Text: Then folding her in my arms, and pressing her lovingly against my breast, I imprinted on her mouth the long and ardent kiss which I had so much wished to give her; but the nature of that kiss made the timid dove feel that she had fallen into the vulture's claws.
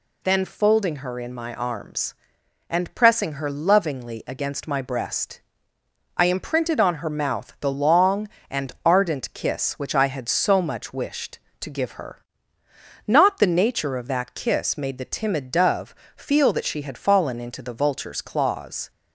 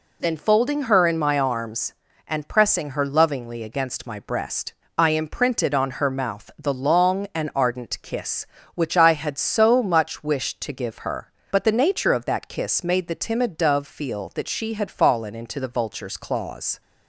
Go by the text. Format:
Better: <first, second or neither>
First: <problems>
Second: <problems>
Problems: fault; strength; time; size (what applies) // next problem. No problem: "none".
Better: second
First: says "not" for "but"; at 13.0 s // pauses between "dove" and "feel"; slight; at 15.9 s; 0.24 s long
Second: none